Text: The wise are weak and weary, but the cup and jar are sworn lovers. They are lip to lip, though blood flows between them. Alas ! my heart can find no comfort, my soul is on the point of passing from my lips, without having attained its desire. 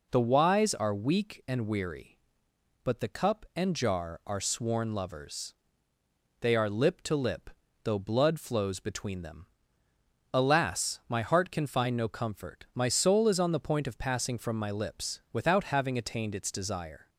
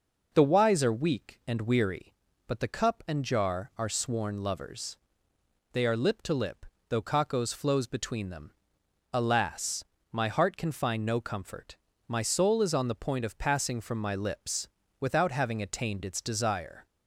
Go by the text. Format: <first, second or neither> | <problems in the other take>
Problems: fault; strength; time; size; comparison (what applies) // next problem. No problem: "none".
first | says "kakos" for "blood"; at 7.0 s